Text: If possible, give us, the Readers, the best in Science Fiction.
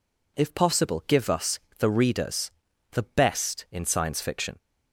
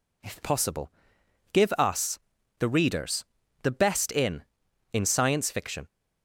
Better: first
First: none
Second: says "in" twice; at 4.9 s

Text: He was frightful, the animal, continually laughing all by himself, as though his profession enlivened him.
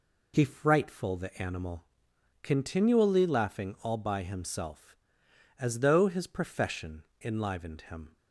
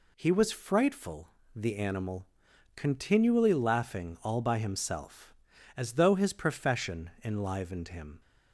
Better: second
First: skips "was"; at 0.4 s // pauses between "profession" and "enlivened"; slight; at 7.0 s; 0.18 s long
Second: none

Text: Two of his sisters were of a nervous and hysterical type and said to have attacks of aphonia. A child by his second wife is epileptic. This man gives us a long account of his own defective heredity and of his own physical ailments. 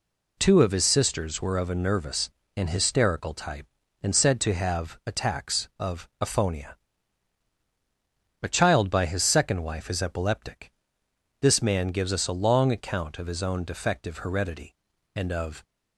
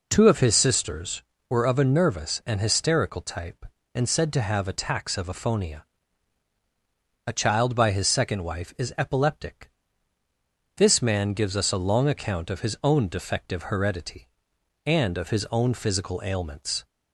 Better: second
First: stops before "his own physical ailments"; at 15.6 s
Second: none

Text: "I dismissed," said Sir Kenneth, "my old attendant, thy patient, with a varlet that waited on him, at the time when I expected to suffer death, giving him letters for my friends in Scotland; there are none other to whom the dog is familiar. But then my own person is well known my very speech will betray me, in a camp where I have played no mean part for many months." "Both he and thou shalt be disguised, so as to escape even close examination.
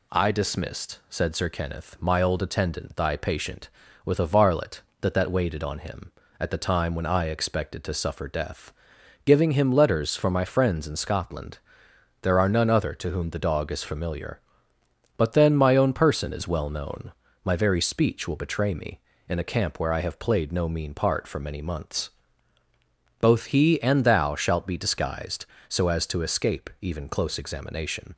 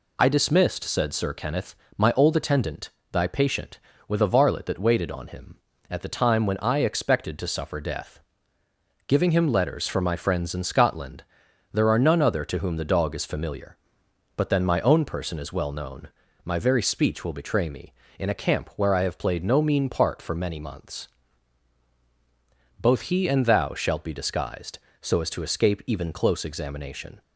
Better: second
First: says "that" twice; at 5.1 s // pauses between "known" and "my"; slight; at 17.1 s; 0.32 s long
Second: pauses between "known" and "my"; slight; at 16.0 s; 0.36 s long

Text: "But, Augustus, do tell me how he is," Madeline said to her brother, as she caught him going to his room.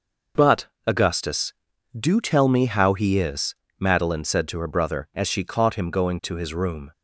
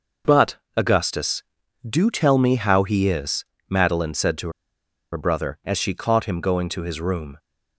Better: first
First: none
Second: pauses between "to" and "her"; noticeable; at 4.4 s; 0.64 s long

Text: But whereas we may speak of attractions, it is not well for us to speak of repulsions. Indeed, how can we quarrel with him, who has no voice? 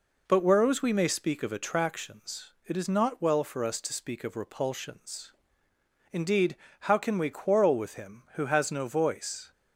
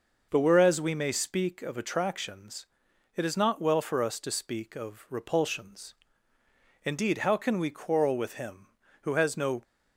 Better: first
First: none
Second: stops before "voice"; at 9.6 s

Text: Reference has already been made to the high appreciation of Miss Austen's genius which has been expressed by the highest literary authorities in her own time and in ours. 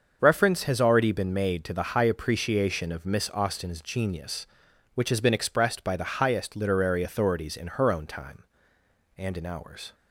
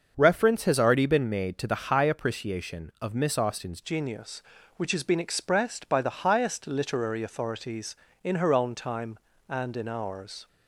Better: first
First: starts louder than the rest; until 1.2 s; 6.5 dB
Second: starts louder than the rest; until 1.1 s; 6.5 dB // changes voice at "genius"; from 3.8 s on; 6.6 s long

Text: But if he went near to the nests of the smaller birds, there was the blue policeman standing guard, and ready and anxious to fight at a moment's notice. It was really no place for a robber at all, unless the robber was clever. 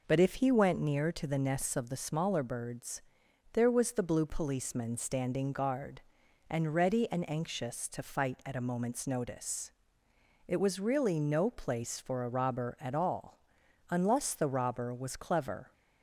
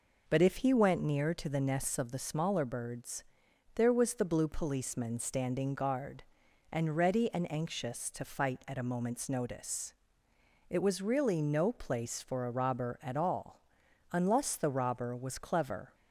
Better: neither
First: none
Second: none

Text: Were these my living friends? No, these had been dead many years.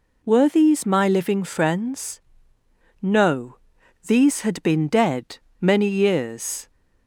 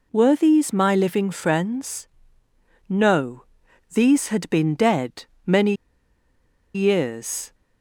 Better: first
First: pauses between "dead" and "many"; slight; at 5.3 s; 0.21 s long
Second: pauses between "dead" and "many"; slight; at 5.2 s; 0.20 s long // pauses between "many" and "years"; at 5.7 s; 1.0 s long

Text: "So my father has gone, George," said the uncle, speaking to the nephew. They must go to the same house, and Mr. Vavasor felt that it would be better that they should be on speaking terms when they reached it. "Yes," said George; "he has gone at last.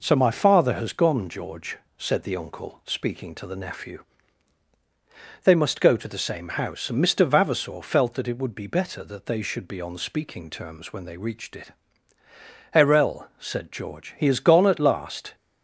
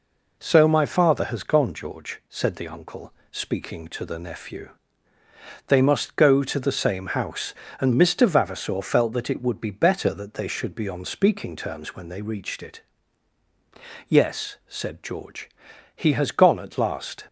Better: second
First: says "Erel" for "Yes"; at 12.7 s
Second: none

